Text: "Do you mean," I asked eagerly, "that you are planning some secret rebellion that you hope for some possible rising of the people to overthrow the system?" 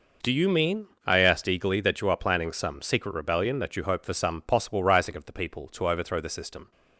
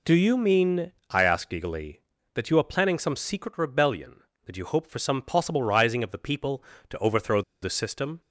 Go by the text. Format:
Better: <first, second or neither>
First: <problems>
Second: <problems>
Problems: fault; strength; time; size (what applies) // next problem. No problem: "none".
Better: first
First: none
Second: pauses between "overthrow" and "the"; slight; at 7.4 s; 0.20 s long